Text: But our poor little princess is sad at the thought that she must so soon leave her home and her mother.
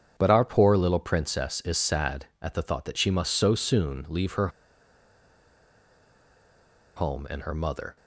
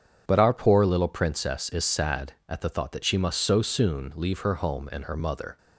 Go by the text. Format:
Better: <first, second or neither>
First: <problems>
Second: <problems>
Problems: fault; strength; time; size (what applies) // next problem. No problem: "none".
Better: second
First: starts louder than the rest; strong; until 1.1 s; 7.5 dB // pauses between "her" and "home"; strong; at 4.4 s; 2.4 s long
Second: starts louder than the rest; strong; until 1.2 s; 7.5 dB